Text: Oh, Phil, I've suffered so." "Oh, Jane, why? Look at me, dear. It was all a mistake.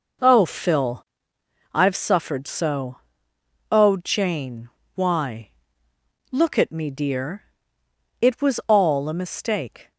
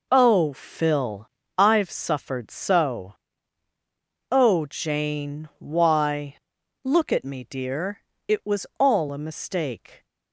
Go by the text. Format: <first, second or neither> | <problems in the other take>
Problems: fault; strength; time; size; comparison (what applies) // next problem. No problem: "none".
neither | none